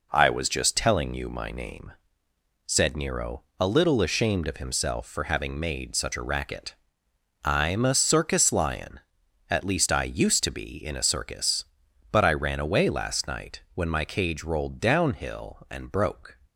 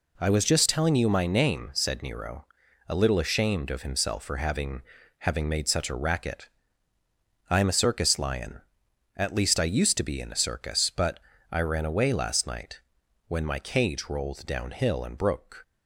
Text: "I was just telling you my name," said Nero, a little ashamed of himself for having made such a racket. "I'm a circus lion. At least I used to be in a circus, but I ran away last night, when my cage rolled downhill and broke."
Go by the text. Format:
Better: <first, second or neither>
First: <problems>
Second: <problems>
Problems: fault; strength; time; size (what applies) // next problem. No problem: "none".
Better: first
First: none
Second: says "having" twice; at 5.1 s // pauses between "but" and "I"; slight; at 11.1 s; 0.32 s long